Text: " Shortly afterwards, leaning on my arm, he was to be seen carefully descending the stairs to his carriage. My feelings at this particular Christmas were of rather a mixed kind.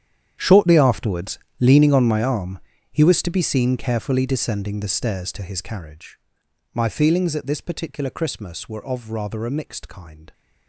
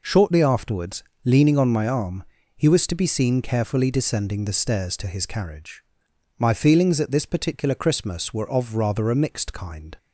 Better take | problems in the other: second | gets quieter; strong; throughout; 16.5 dB

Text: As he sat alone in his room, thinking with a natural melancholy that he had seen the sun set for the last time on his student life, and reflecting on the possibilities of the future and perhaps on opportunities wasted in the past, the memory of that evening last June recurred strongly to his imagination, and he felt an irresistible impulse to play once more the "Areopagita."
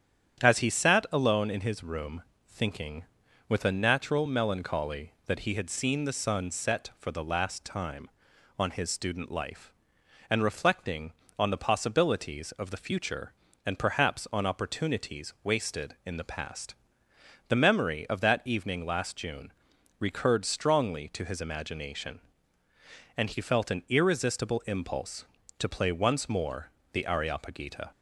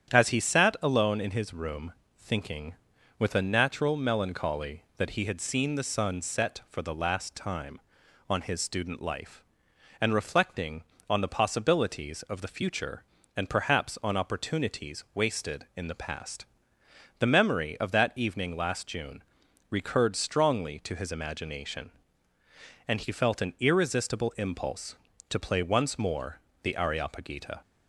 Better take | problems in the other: neither | starts louder than the rest; strong; the same in both // pauses between "June" and "recurred"; noticeable; the same in both // pauses between "more" and "the"; slight; the same in both

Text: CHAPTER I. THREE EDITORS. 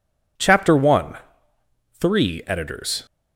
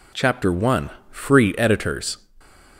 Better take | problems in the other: first | says "Free" for "THREE"; at 1.0 s

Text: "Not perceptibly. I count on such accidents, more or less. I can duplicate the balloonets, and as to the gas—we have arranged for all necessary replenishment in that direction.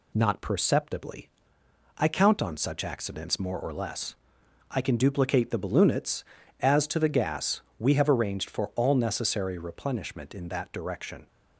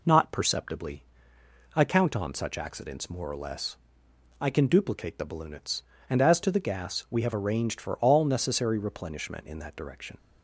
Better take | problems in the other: second | skips "and"; at 6.4 s

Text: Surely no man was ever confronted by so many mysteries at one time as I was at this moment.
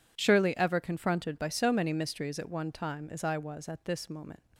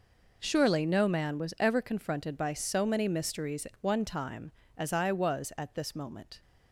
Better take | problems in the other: second | skips "no man was"; at 0.5 s

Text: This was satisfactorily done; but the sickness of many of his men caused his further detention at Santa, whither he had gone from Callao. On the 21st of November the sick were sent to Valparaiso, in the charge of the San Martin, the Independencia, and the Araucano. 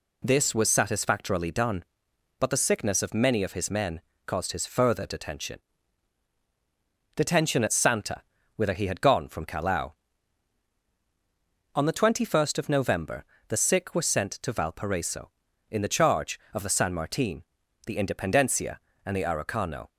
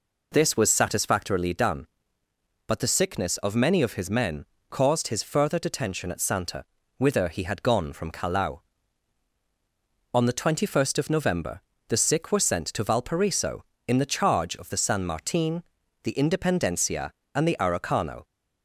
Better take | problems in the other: second | pauses between "men" and "caused"; slight; at 3.9 s; 0.26 s long; slight in the second // says "detention" twice; at 7.1 s // pauses between "November" and "the"; slight; at 13.2 s; 0.24 s long; slight in the second

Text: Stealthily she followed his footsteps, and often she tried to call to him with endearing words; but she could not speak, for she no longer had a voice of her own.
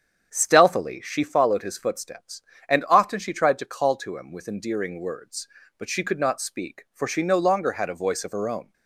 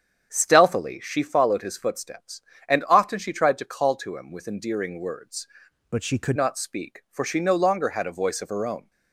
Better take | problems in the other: first | starts louder than the rest; strong; until 1.3 s; 8 dB; strong in the first // changes voice from "but" to "could"; from 5.9 to 6.3 s; 0.4 s long

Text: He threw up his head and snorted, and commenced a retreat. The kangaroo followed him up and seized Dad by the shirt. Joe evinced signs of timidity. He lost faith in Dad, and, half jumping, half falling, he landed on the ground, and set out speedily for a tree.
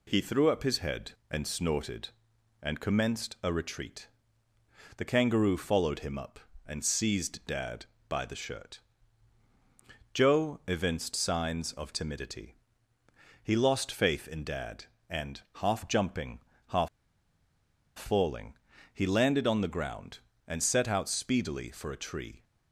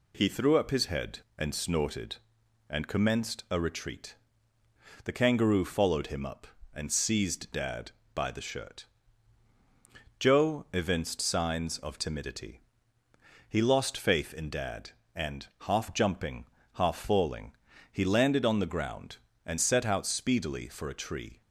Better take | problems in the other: second | pauses between "half" and "falling"; at 16.8 s; 1.0 s long

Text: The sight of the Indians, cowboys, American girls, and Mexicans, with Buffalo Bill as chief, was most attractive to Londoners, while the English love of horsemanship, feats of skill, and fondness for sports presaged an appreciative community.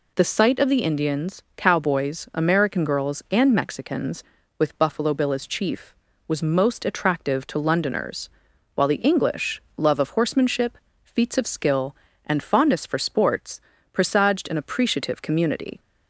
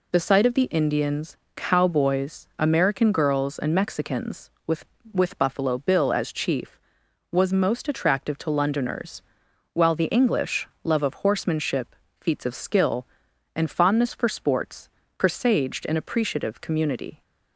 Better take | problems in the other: first | says "with" twice; at 5.1 s // pauses between "English" and "love"; slight; at 10.6 s; 0.16 s long; slight in the first // pauses between "sports" and "presaged"; slight; at 14.8 s; 0.28 s long; slight in the first

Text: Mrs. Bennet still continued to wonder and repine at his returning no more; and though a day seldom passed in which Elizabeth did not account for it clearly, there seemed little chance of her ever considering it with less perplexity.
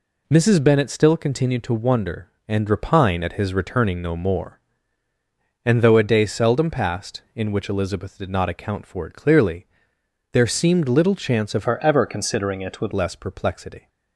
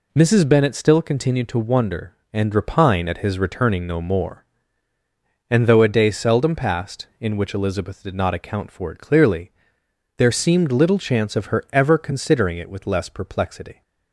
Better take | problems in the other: second | changes voice from "her" to "with"; from 11.6 to 12.9 s; 1.3 s long

